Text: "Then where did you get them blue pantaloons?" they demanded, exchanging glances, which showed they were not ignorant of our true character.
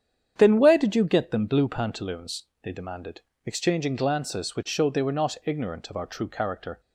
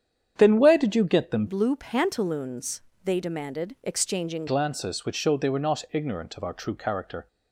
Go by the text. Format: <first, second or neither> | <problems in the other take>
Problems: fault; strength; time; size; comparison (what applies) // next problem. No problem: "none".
first | starts louder than the rest; strong; until 1.3 s; 8.5 dB; strong in the first // changes voice from "blue" to "exchanging"; from 1.4 to 4.4 s; 3.0 s long